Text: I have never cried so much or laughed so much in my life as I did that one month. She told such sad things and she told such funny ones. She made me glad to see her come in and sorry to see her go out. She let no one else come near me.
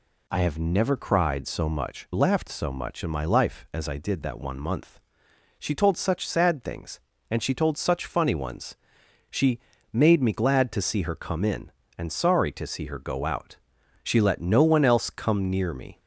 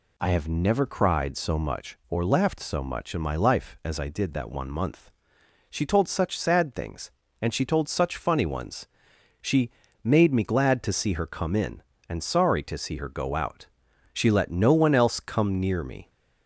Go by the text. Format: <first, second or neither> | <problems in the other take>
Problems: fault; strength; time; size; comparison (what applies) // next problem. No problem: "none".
second | skips "or"; at 2.1 s // pauses between "She" and "made"; slight; at 9.5 s; 0.32 s long; slight in the second